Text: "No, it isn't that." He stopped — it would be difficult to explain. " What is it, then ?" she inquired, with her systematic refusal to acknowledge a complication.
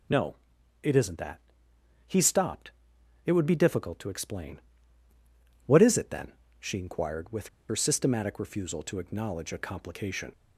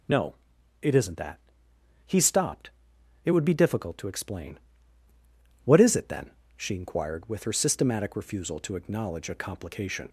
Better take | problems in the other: second | pauses between "with" and "her"; slight; at 7.4 s; 0.22 s long

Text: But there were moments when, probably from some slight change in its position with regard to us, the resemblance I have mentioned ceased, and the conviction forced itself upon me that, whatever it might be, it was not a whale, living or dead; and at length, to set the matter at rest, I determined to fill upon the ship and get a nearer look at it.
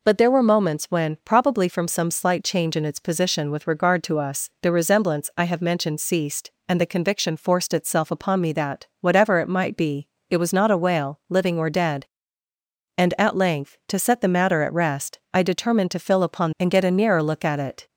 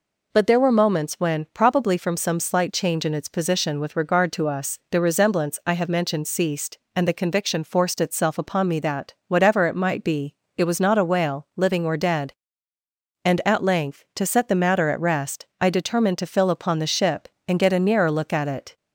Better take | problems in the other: second | skips "the ship"; at 16.5 s

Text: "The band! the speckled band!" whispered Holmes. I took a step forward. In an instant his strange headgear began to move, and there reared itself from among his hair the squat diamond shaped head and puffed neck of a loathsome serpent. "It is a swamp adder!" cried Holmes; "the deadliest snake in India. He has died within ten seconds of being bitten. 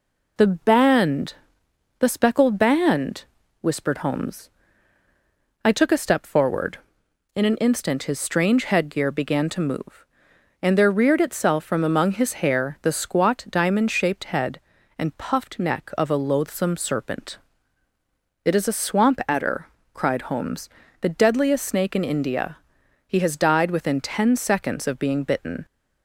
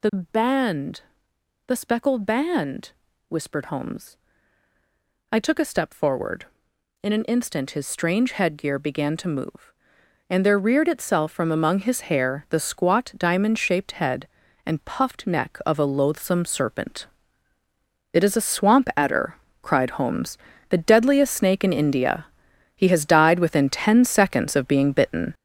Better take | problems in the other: first | gets louder; throughout; 7 dB

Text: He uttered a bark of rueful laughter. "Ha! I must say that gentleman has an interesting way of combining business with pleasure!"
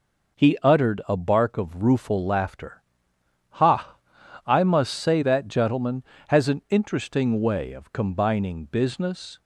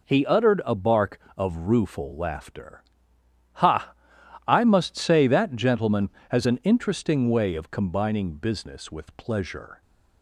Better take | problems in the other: second | stops before "with pleasure"; at 9.3 s

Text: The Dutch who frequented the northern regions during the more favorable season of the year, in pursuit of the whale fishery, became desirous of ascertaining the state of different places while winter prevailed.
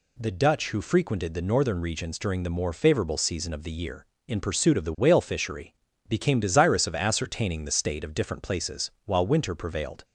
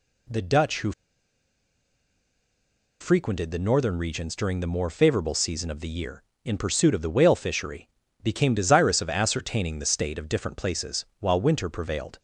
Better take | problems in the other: first | pauses between "who" and "frequented"; strong; at 0.9 s; 2.0 s long // pauses between "places" and "while"; slight; at 11.0 s; 0.16 s long; slight in the first

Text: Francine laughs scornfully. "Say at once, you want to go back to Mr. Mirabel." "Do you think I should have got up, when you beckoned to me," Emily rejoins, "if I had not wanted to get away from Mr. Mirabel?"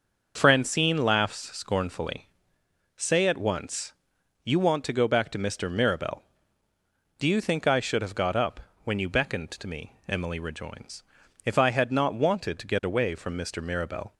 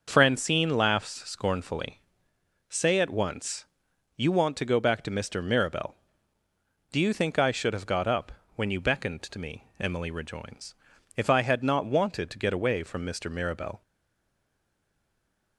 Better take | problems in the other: first | starts louder than the rest; until 1.0 s; 6 dB; also in the first // stays silent after the last word; noticeable; from 13.8 s on; 1.7 s long

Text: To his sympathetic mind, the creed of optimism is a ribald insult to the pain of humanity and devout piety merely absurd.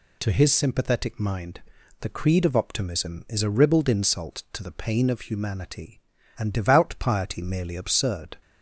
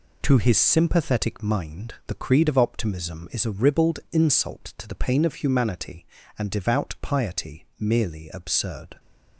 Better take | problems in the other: neither | none

